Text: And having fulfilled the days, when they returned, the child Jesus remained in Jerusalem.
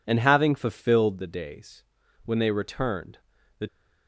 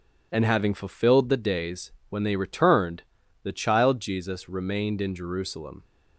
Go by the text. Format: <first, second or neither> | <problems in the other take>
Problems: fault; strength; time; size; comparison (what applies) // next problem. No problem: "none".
second | stops before "child Jesus remained in Jerusalem"; at 3.6 s